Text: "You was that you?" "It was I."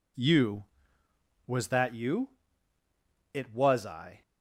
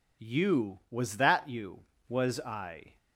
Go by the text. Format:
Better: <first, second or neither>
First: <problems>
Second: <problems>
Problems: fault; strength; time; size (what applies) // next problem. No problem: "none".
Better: first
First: none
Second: skips "It"; at 1.9 s